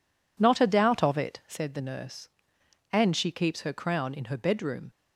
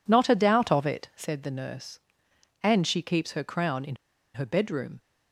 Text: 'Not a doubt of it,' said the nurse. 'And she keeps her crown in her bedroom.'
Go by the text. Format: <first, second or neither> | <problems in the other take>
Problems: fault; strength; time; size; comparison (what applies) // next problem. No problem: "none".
first | pauses between "in" and "her"; at 3.9 s; 0.38 s long